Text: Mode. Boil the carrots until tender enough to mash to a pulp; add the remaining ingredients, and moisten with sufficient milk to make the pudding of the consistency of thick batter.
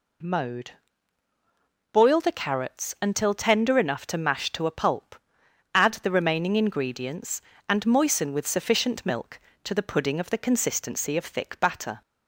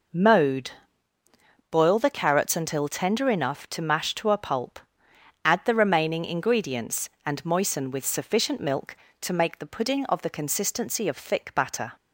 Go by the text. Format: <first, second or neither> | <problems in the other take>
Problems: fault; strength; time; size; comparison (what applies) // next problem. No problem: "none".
second | skips "make"; at 9.7 s